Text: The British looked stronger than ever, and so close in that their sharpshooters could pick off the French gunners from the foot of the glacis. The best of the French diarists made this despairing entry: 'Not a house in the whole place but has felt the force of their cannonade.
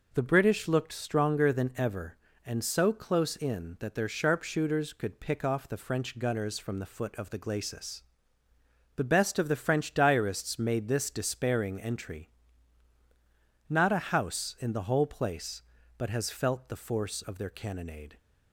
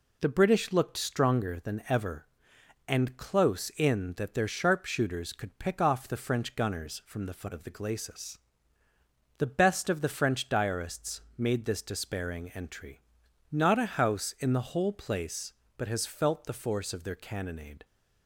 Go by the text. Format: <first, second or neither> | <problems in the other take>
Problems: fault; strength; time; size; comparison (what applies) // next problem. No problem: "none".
first | skips "so"; at 3.1 s // pauses between "diarists" and "made"; slight; at 11.2 s; 0.16 s long